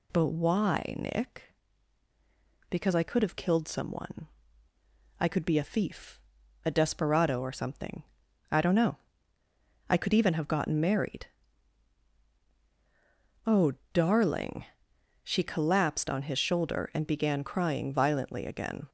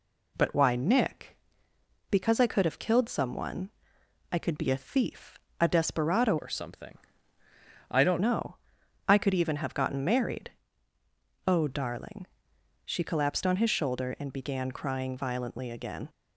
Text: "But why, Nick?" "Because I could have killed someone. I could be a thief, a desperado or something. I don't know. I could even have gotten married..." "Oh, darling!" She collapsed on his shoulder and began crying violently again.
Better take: first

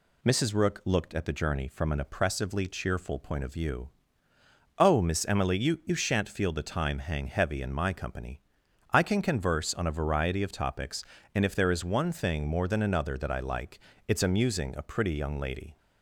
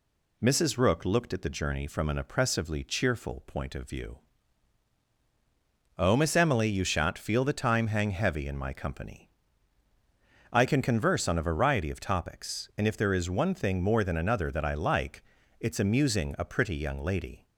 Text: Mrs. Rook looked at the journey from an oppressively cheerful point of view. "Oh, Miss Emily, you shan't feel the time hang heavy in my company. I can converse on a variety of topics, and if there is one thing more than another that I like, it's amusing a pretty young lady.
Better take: second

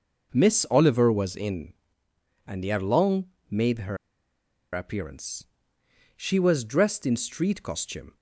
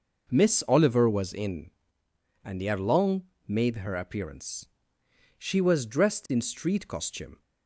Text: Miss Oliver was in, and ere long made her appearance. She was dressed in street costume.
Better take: second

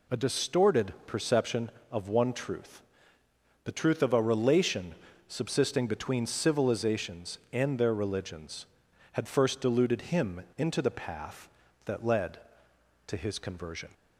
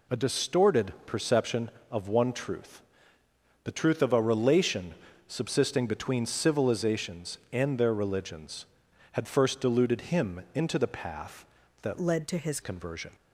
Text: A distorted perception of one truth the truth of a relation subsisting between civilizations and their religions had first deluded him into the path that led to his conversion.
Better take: first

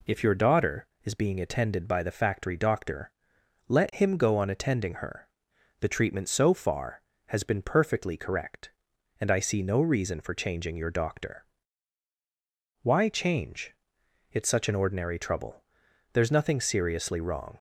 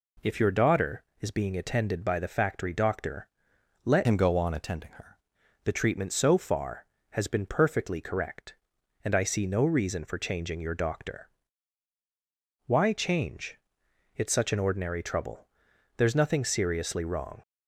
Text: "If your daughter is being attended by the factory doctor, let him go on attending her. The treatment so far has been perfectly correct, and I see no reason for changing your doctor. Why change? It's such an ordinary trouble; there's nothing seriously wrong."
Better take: first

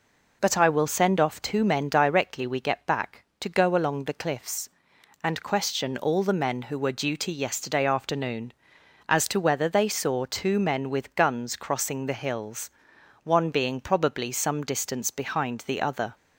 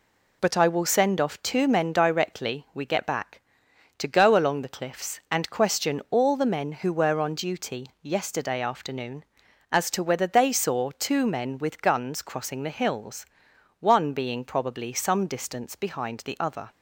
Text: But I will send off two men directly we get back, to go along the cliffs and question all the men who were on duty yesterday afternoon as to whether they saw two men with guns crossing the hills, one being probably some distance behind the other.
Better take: second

